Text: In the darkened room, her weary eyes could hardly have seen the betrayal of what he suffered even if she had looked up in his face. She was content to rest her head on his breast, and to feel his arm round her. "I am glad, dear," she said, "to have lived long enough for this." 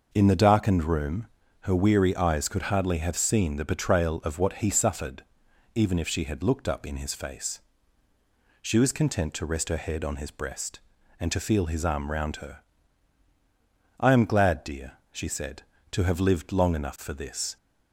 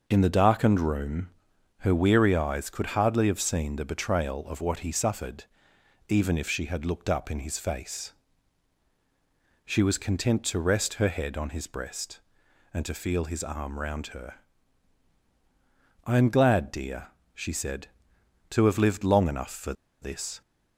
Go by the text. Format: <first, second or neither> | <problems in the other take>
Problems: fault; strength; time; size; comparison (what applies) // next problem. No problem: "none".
first | pauses between "suffered" and "even"; noticeable; at 5.4 s; 0.64 s long; noticeable in the first // pauses between "for" and "this"; slight; at 19.7 s; 0.29 s long